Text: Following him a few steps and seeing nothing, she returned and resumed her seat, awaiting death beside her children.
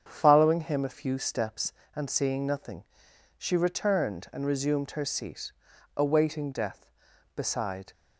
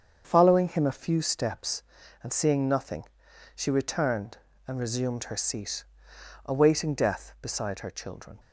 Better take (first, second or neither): second